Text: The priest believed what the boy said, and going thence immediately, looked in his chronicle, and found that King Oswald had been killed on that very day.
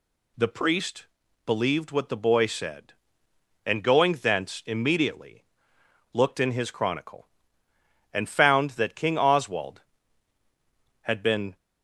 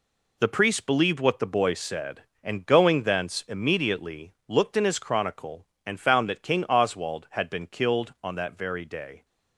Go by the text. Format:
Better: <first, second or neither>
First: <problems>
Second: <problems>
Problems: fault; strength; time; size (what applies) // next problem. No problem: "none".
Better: second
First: pauses between "priest" and "believed"; at 1.0 s; 0.40 s long // stops before "killed on that very day"; at 11.5 s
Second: none